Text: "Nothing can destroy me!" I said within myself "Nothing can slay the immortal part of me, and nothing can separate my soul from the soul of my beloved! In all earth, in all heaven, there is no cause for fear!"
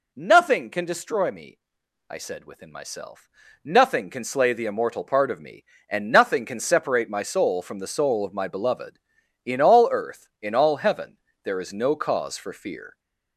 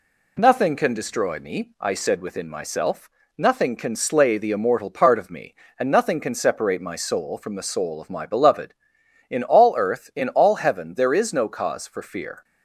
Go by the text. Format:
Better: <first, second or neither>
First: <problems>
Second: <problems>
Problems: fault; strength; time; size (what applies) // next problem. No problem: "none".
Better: second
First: gets louder; slight; throughout; 3 dB // pauses between "myself" and "Nothing"; slight; at 3.3 s; 0.34 s long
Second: pauses between "myself" and "Nothing"; slight; at 3.0 s; 0.28 s long